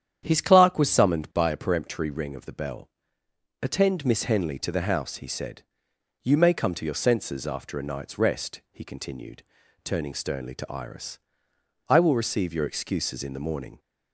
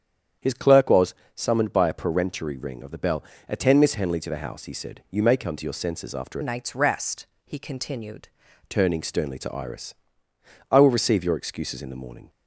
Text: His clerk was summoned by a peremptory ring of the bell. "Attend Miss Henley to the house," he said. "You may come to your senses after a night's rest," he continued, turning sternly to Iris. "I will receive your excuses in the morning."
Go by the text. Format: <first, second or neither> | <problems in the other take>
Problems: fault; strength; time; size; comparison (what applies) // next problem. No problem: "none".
first | starts louder than the rest; strong; until 1.6 s; 8.5 dB; strong in the first // pauses between "was" and "summoned"; slight; at 1.1 s; 0.20 s long // changes voice from "night's" to "continued"; from 6.4 to 8.2 s; 1.8 s long